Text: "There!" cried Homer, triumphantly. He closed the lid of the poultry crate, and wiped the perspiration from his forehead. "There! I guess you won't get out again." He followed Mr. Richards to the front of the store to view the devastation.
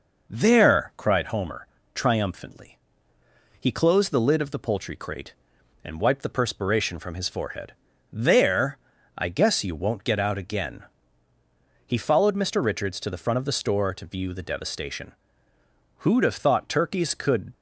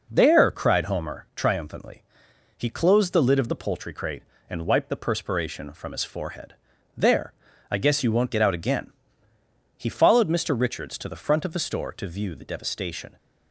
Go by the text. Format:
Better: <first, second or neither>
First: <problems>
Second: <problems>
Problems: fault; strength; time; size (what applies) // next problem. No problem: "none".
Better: second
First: goes on to say "Who'd have thought turkeys could"; from 15.9 s on; 1.5 s long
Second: none